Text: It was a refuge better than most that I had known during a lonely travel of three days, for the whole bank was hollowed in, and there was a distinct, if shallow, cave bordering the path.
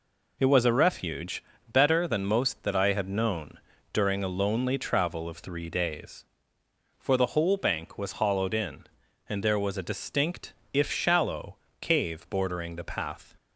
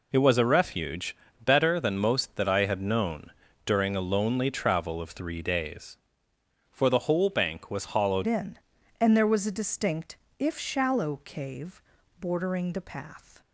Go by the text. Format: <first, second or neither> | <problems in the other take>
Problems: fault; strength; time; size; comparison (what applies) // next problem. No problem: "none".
first | pauses between "refuge" and "better"; slight; at 1.1 s; 0.28 s long; slight in the first // pauses between "known" and "during"; slight; at 3.3 s; 0.32 s long; slight in the first // changes voice at "in"; from 8.2 s on; 5.2 s long // pauses between "cave" and "bordering"; at 11.8 s; 0.38 s long